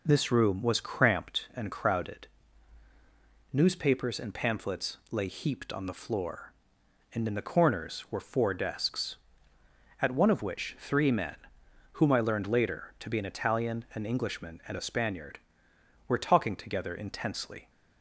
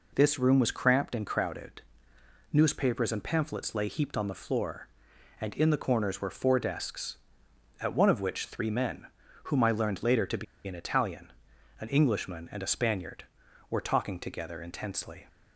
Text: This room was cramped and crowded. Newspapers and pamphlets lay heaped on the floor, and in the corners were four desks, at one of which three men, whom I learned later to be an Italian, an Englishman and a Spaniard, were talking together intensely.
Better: first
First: none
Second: pauses between "be" and "an"; slight; at 10.4 s; 0.22 s long

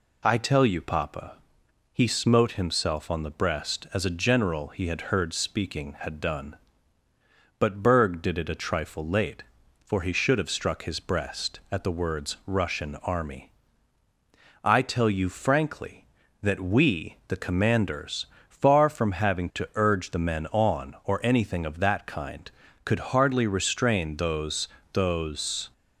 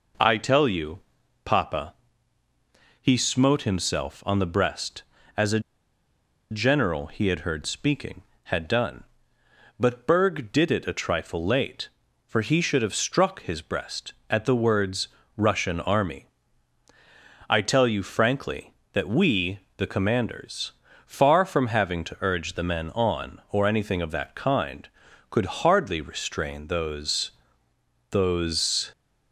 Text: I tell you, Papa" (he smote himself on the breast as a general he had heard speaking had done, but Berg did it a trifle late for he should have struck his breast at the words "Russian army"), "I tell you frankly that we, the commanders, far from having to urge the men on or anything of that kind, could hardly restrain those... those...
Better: first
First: none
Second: pauses between "a" and "general"; noticeable; at 5.5 s; 0.91 s long // pauses between "words" and "Russian"; slight; at 15.0 s; 0.28 s long

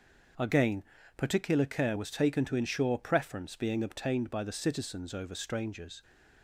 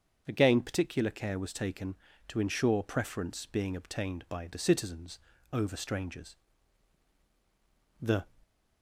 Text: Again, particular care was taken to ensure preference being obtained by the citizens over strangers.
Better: first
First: starts louder than the rest; until 1.7 s; 6 dB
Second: starts louder than the rest; until 1.2 s; 7 dB // pauses between "citizens" and "over"; slight; at 5.1 s; 0.33 s long // goes on to say "The"; slight; from 8.0 s on; 0.30 s long

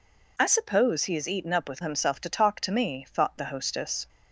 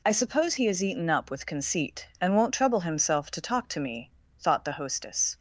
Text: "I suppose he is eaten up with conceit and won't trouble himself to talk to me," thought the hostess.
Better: second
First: skips "conceit and won't trouble"; at 1.8 s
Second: none

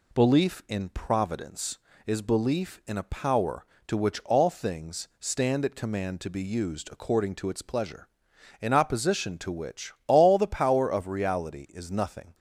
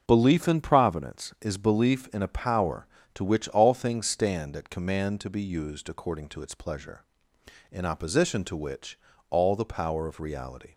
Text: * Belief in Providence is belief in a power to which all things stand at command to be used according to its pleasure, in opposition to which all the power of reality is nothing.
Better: first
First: none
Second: starts louder than the rest; until 1.0 s; 6 dB // pauses between "which" and "all"; slight; at 8.9 s; 0.32 s long // stops before "is nothing"; at 10.7 s

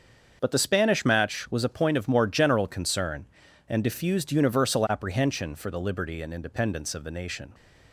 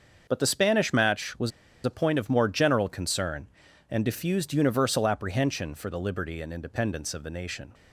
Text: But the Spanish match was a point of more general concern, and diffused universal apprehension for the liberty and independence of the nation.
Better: first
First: starts louder than the rest; until 1.4 s; 7 dB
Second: starts louder than the rest; until 1.2 s; 6.5 dB // pauses between "was" and "a"; slight; at 1.5 s; 0.34 s long

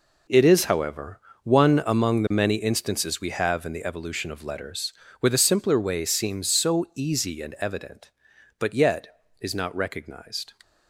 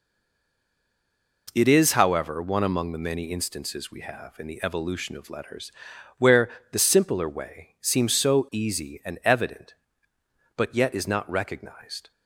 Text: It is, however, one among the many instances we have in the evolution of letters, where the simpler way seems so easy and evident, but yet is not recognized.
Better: first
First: none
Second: stays silent before the first word; noticeable; until 1.4 s; 1.4 s long // pauses between "where" and "the"; slight; at 6.4 s; 0.24 s long

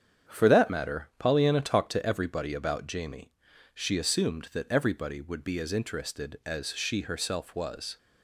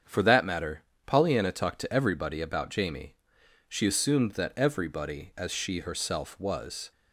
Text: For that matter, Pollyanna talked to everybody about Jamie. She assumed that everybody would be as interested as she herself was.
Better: first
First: starts louder than the rest; strong; until 1.3 s; 8 dB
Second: starts louder than the rest; strong; until 1.3 s; 7.5 dB // skips "would be as interested"; at 5.3 s

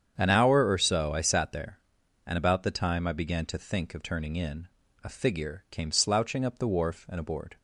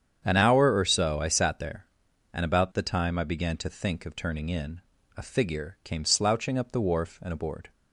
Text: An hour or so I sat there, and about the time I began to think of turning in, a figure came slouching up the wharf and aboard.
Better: neither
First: starts louder than the rest; strong; until 1.1 s; 8 dB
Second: starts louder than the rest; strong; until 1.2 s; 8 dB

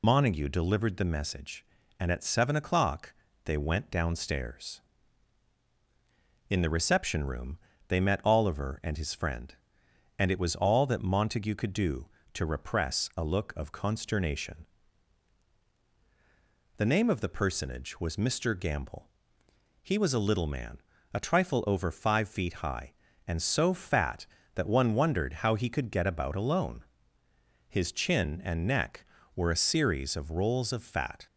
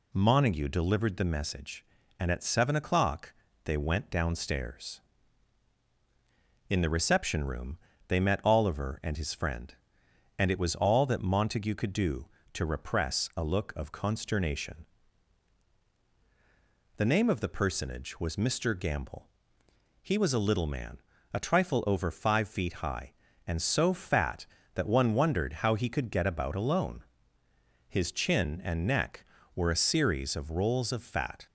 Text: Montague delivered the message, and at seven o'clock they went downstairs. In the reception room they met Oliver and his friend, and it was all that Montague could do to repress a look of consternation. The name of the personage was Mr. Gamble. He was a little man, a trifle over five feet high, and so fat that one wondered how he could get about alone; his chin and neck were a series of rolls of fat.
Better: second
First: loses the start of "Montague"; at 0.0 s; 95 ms // pauses between "o'clock" and "they"; slight; at 3.1 s; 0.32 s long // pauses between "room" and "they"; slight; at 7.5 s; 0.30 s long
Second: pauses between "o'clock" and "they"; slight; at 3.3 s; 0.32 s long // pauses between "room" and "they"; slight; at 7.7 s; 0.30 s long

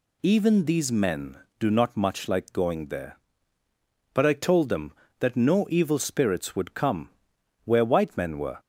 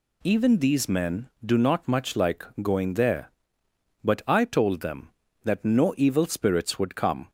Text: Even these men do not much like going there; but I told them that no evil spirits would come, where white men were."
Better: first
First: none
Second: pauses between "like" and "going"; slight; at 2.4 s; 0.18 s long // stops before "where white men were"; at 7.2 s

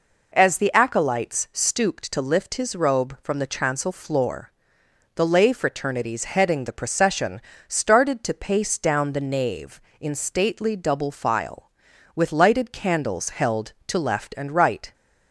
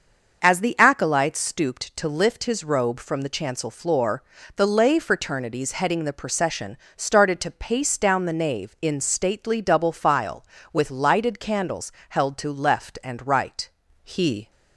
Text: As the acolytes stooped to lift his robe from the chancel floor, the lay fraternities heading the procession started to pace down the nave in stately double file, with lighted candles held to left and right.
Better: first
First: pauses between "procession" and "started"; slight; at 7.3 s; 0.28 s long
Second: starts louder than the rest; until 1.4 s; 6.5 dB // pauses between "procession" and "started"; slight; at 6.7 s; 0.18 s long // pauses between "candles" and "held"; slight; at 11.9 s; 0.18 s long // goes on to say "He"; slight; from 14.0 s on; 0.48 s long

